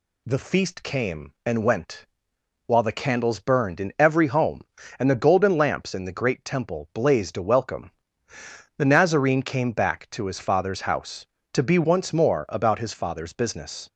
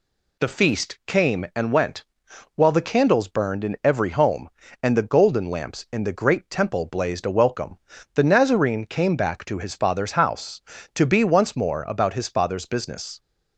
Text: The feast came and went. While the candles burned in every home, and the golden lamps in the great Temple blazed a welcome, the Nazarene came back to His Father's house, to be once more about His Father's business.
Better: neither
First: none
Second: none

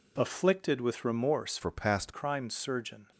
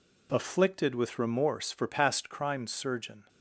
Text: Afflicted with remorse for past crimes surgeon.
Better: second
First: changes voice from "for" to "past"; from 1.6 to 2.1 s; 0.5 s long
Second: none

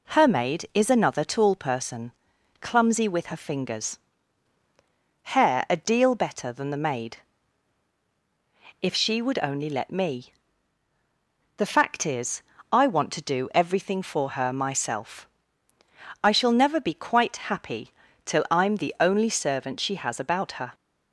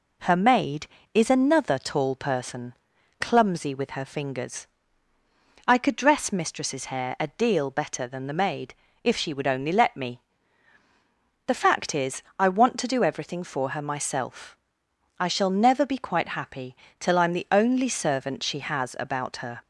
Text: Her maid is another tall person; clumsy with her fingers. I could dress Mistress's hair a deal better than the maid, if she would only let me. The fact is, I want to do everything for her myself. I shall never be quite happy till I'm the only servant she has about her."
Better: second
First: skips "I could dress Mistress's"; at 4.6 s // pauses between "happy" and "till"; slight; at 17.9 s; 0.32 s long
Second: pauses between "happy" and "till"; slight; at 16.7 s; 0.24 s long

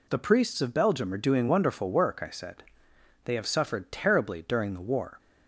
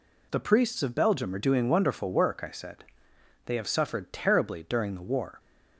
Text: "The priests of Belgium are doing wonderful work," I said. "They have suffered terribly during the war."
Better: neither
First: none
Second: none

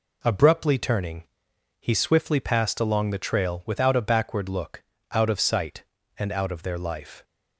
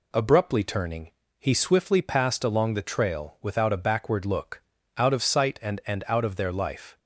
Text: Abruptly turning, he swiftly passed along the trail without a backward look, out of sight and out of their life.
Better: first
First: none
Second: says "and" twice; at 5.8 s

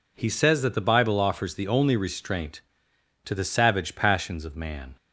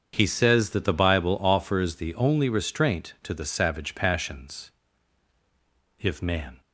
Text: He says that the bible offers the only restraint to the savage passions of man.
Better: first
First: none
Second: starts louder than the rest; strong; until 1.1 s; 7 dB // says "if" for "of"; at 5.9 s

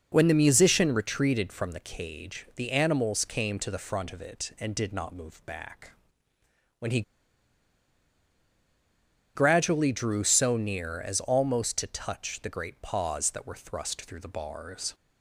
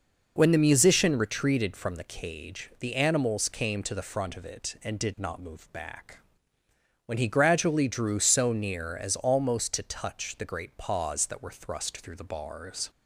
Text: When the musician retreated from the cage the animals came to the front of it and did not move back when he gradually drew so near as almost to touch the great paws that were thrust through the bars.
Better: second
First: pauses between "back" and "when"; noticeable; at 5.9 s; 0.84 s long // pauses between "he" and "gradually"; strong; at 7.0 s; 2.3 s long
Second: pauses between "back" and "when"; noticeable; at 6.1 s; 0.84 s long

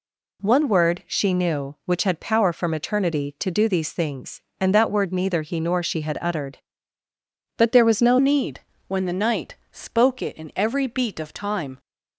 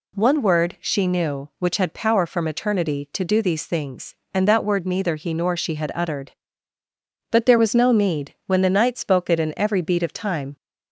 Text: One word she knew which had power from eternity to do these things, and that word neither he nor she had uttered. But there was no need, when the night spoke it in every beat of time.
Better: second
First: changes voice at "need"; from 8.1 s on; 3.6 s long // pauses between "night" and "spoke"; slight; at 9.5 s; 0.18 s long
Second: none

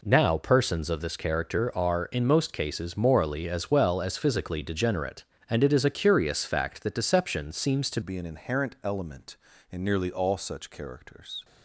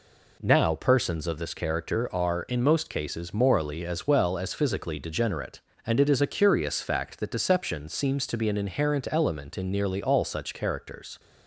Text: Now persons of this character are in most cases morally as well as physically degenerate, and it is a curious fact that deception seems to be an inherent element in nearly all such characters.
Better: second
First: changes voice at "be"; from 8.0 s on; 3.4 s long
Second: none

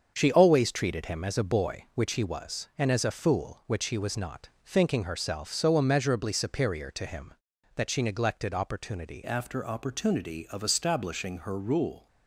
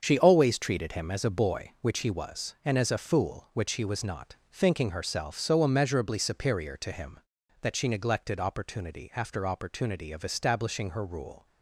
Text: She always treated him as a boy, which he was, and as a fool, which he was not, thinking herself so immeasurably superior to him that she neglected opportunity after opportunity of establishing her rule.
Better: second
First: starts louder than the rest; until 1.1 s; 7 dB // changes voice at "after"; from 9.2 s on; 2.8 s long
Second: starts louder than the rest; until 1.0 s; 7 dB

